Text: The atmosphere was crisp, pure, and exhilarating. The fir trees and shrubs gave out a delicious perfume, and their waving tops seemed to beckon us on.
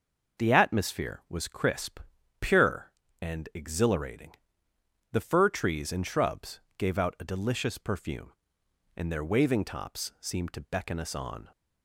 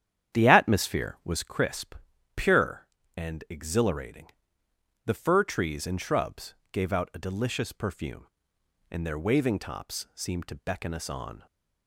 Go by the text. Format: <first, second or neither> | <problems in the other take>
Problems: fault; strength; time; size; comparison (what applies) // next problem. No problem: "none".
first | starts louder than the rest; strong; until 1.6 s; 9.5 dB // pauses between "shrubs" and "gave"; slight; at 6.5 s; 0.16 s long; slight in the first